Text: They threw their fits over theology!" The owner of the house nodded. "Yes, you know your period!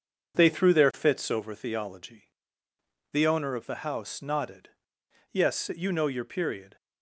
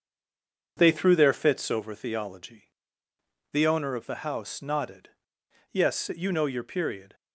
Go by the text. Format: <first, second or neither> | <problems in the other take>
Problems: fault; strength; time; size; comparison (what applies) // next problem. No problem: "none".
first | stays silent before the first word; slight; until 0.7 s; 0.7 s long